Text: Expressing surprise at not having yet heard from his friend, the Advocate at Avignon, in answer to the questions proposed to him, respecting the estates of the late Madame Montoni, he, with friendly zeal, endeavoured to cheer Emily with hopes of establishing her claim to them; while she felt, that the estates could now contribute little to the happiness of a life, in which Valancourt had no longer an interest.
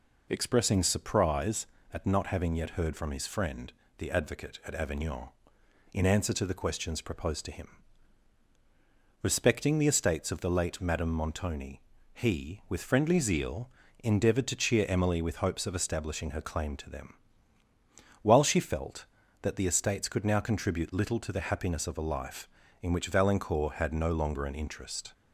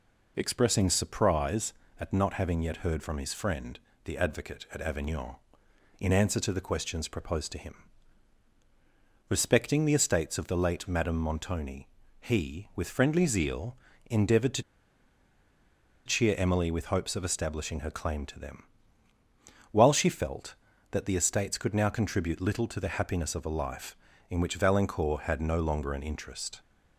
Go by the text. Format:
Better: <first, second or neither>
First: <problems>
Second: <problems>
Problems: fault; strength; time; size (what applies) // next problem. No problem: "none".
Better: first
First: none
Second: pauses between "to" and "cheer"; strong; at 14.6 s; 1.4 s long